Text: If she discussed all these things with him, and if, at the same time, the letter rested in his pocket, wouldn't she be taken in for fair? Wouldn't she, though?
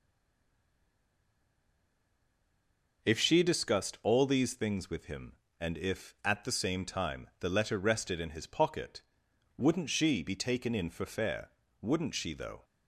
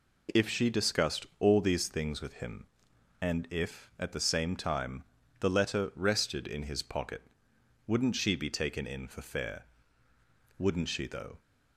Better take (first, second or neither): second